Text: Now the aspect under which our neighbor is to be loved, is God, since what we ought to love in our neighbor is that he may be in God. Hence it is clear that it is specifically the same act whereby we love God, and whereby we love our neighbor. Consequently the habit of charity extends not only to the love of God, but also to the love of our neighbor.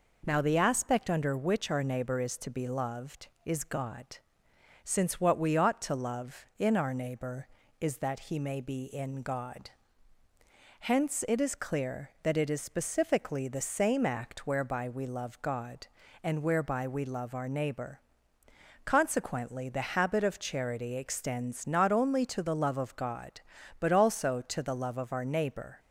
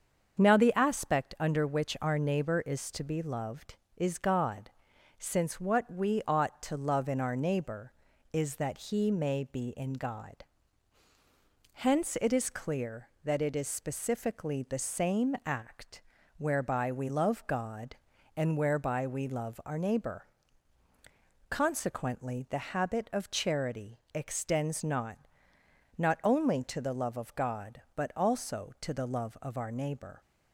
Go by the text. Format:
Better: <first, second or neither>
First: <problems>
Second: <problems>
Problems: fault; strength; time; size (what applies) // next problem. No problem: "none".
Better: first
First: none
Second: starts louder than the rest; until 1.4 s; 7 dB // pauses between "act" and "whereby"; slight; at 16.0 s; 0.36 s long // says "not" twice; at 25.9 s